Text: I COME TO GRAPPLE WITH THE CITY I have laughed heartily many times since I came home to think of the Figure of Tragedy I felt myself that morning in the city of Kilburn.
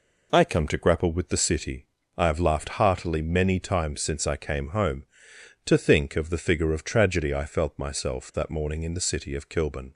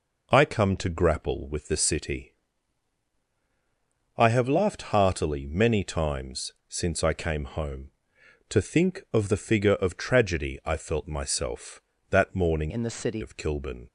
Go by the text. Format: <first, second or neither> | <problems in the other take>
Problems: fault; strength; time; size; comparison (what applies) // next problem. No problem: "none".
first | pauses between "CITY" and "I"; strong; at 2.3 s; 1.8 s long; slight in the first // pauses between "times" and "since"; slight; at 6.5 s; 0.16 s long // changes voice from "in" to "city"; from 12.6 to 13.2 s; 0.6 s long